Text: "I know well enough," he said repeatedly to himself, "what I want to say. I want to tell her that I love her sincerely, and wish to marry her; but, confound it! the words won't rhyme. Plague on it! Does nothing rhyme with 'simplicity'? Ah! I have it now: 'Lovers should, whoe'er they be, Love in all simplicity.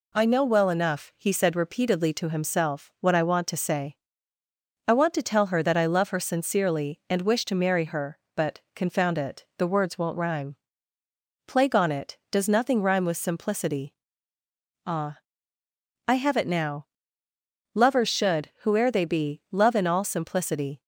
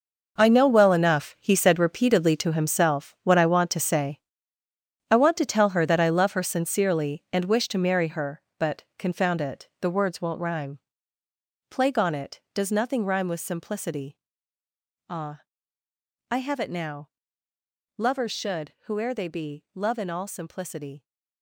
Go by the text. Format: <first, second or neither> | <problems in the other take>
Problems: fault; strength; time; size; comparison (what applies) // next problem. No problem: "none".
first | gets quieter; strong; throughout; 13 dB